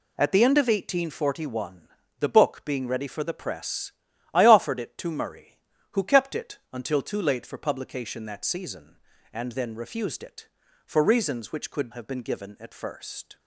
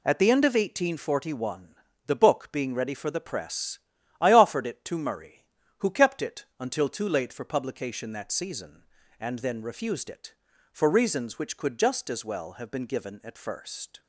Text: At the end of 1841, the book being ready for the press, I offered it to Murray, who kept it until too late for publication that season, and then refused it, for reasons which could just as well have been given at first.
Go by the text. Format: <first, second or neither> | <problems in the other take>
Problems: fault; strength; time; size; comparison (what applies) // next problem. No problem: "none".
second | skips "just as well"; at 11.9 s